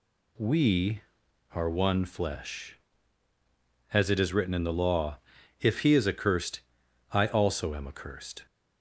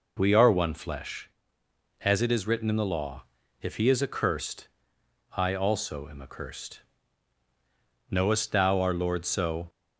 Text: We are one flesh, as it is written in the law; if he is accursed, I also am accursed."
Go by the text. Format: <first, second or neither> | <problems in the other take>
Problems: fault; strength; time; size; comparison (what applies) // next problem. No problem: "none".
first | goes on to say "Knowest thou our Lord so"; from 8.0 s on; 1.5 s long